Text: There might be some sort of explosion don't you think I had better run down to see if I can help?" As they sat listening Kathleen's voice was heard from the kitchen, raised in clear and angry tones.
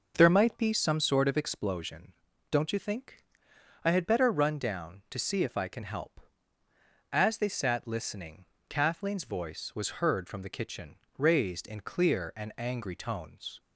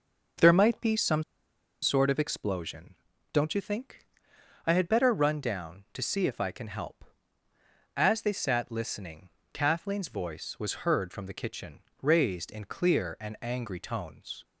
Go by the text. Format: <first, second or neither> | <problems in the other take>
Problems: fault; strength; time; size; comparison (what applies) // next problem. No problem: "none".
first | pauses between "some" and "sort"; noticeable; at 1.2 s; 0.60 s long // pauses between "explosion" and "don't"; slight; at 2.9 s; 0.36 s long; slight in the first // pauses between "think" and "I"; noticeable; at 4.0 s; 0.58 s long; noticeable in the first // pauses between "listening" and "Kathleen's"; slight; at 9.2 s; 0.24 s long; slight in the first